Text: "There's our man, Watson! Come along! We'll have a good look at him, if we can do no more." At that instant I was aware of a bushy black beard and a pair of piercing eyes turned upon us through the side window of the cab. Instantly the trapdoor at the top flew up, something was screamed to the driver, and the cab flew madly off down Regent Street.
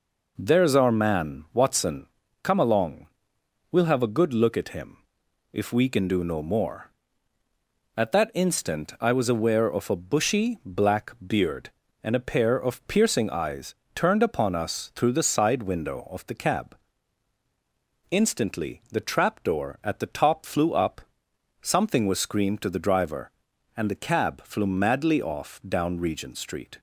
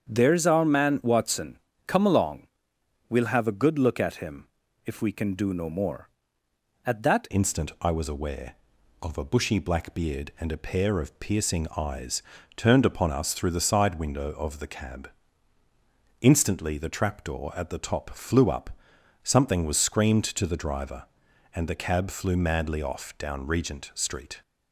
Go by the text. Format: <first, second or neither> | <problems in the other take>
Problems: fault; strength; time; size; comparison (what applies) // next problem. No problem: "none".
first | starts louder than the rest; strong; until 1.1 s; 7.5 dB // changes voice at "instant"; from 7.3 s on; 17.1 s long // pauses between "eyes" and "turned"; slight; at 12.2 s; 0.32 s long; slight in the first